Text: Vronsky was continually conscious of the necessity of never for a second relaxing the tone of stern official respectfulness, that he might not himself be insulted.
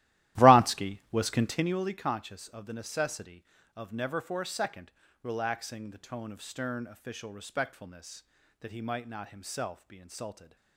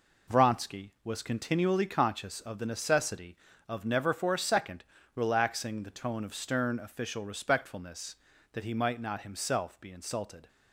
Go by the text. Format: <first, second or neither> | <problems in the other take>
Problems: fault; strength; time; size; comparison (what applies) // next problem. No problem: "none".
second | starts louder than the rest; strong; until 1.8 s; 15.5 dB // pauses between "second" and "relaxing"; slight; at 4.9 s; 0.32 s long; slight in the second